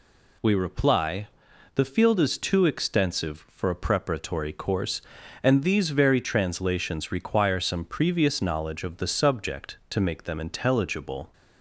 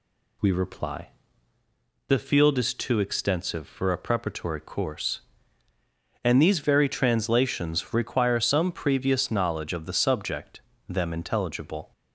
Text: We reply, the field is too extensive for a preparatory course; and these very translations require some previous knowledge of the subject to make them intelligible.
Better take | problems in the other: first | skips "to make"; at 10.7 s

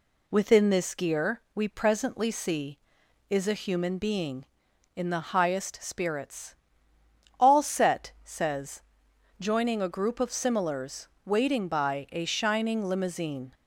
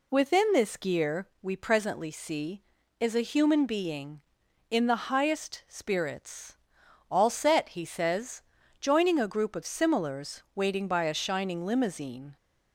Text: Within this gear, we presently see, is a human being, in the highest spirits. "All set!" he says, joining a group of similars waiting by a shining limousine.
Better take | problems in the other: second | skips "he"; at 8.1 s // pauses between "similars" and "waiting"; slight; at 11.0 s; 0.16 s long

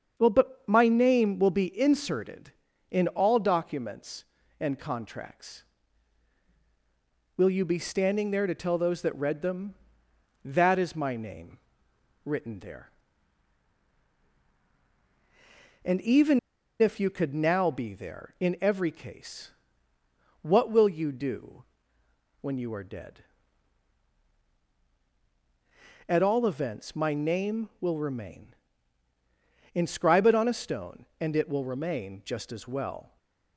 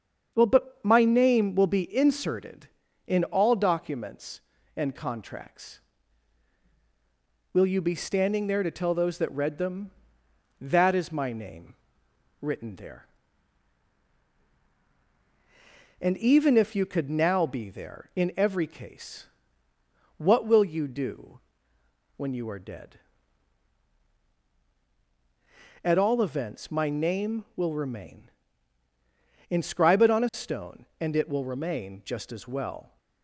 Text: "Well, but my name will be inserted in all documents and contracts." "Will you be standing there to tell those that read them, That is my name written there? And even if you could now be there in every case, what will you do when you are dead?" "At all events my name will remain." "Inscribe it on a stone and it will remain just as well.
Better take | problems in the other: second | starts louder than the rest; strong; until 1.1 s; 7 dB; strong in the second // pauses between "name" and "written"; noticeable; at 11.5 s; 0.66 s long; noticeable in the second // pauses between "even" and "if"; at 16.3 s; 0.42 s long // pauses between "do" and "when"; noticeable; at 21.6 s; 0.74 s long; noticeable in the second // stays silent after the last word; slight; from 33.0 s on; 0.5 s long

